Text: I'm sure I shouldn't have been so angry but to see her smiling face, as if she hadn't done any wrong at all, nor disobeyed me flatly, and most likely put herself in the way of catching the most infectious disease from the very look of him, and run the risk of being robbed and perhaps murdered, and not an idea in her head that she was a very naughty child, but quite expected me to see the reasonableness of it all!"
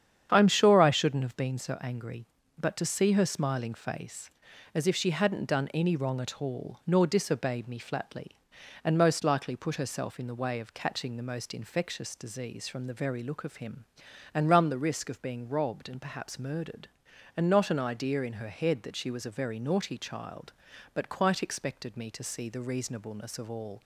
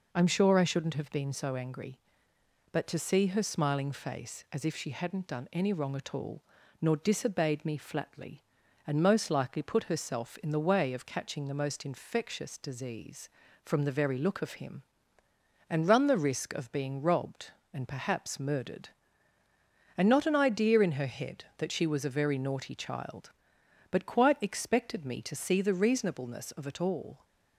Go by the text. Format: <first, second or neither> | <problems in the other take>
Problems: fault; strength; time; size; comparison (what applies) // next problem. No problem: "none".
second | starts louder than the rest; strong; until 1.3 s; 8.5 dB // skips "it"; at 23.4 s